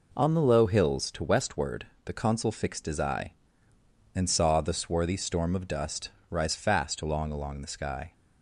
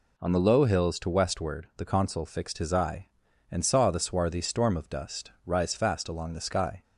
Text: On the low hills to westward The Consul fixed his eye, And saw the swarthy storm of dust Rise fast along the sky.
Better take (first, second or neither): second